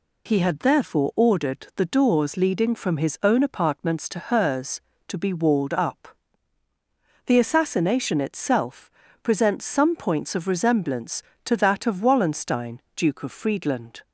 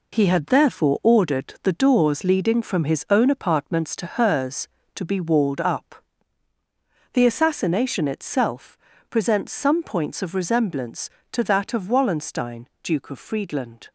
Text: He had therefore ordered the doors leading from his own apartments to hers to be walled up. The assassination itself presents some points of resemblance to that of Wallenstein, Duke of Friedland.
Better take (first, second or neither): first